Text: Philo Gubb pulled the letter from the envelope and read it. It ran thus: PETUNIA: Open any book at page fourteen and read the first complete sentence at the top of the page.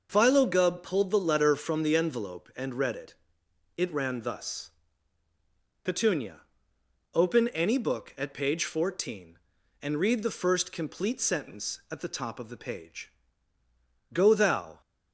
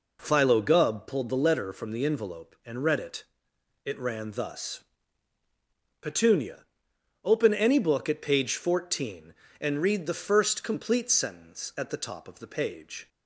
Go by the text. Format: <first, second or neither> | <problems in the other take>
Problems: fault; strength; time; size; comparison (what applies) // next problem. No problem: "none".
second | goes on to say "Go thou"; noticeable; from 14.1 s on; 0.68 s long